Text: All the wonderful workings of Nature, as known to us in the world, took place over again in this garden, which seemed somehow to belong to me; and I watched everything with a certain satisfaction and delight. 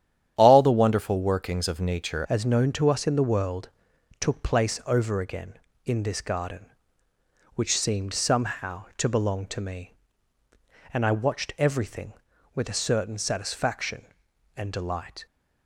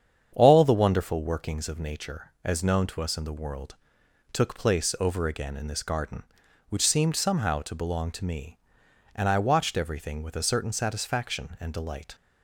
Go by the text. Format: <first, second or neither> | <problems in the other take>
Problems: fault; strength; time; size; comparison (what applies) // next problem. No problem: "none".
second | starts louder than the rest; strong; until 1.3 s; 10 dB; strong in the second // changes voice at "as"; from 2.2 s on; 13.0 s long